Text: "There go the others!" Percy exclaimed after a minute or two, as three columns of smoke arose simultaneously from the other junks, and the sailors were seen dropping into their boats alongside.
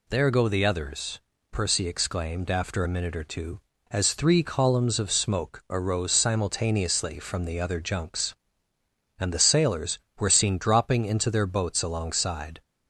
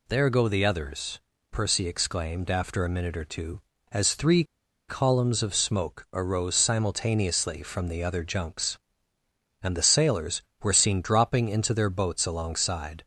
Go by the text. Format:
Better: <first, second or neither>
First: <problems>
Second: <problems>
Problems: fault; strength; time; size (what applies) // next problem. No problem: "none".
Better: first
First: none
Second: pauses between "three" and "columns"; at 4.4 s; 0.44 s long